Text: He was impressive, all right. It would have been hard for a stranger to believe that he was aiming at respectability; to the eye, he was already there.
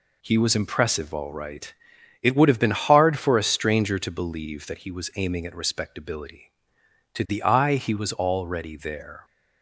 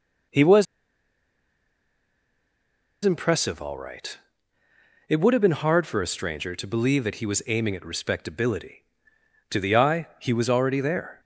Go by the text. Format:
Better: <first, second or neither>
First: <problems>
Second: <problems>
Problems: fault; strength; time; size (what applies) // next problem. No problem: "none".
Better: first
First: none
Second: pauses between "was" and "impressive"; strong; at 0.6 s; 2.3 s long